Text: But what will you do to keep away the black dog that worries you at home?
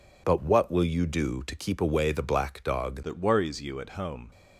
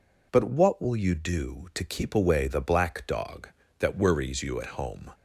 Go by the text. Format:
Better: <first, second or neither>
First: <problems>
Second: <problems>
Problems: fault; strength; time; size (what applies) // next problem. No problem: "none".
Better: second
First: changes voice at "that"; from 3.0 s on; 1.3 s long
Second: none